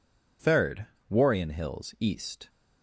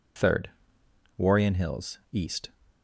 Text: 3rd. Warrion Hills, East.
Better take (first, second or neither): neither